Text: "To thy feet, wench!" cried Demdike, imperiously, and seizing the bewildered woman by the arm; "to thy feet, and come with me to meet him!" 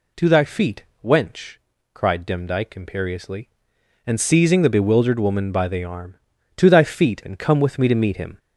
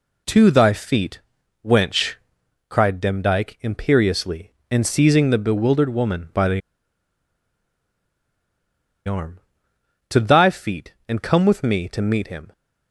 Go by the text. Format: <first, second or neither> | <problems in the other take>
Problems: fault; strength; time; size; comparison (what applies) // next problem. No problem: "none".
first | pauses between "the" and "arm"; strong; at 6.6 s; 2.4 s long